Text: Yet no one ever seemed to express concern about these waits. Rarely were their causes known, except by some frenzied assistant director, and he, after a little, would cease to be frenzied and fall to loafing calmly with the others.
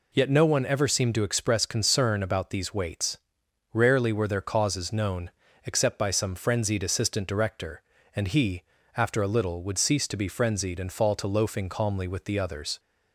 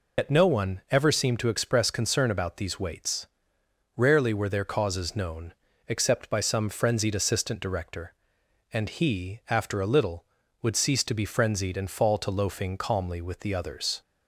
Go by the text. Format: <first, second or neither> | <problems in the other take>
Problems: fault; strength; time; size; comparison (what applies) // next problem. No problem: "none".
first | loses the start of "Yet"; at 0.1 s; 95 ms